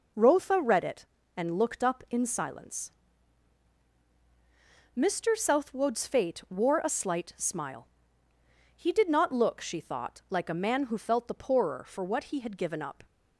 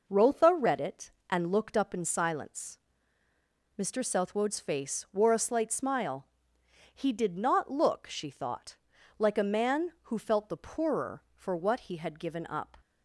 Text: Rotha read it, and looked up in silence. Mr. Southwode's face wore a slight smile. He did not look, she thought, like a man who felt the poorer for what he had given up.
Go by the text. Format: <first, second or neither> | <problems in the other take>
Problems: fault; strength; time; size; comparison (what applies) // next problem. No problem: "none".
second | says "fate" for "face"; at 6.0 s